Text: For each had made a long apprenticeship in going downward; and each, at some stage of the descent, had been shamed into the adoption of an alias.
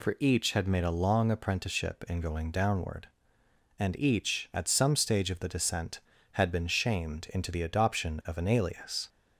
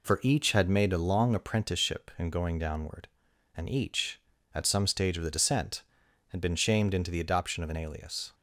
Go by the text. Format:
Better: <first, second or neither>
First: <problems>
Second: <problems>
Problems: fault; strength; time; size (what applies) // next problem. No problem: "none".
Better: neither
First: none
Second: none